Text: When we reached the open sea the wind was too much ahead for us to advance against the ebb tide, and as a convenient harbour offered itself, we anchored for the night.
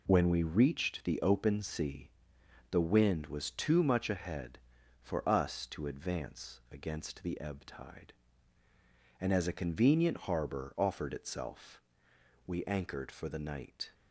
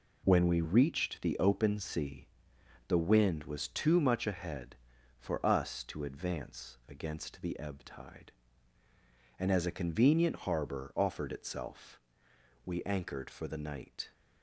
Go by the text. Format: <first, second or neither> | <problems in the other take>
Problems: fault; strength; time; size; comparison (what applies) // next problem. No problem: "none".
neither | pauses between "sea" and "the"; noticeable; the same in both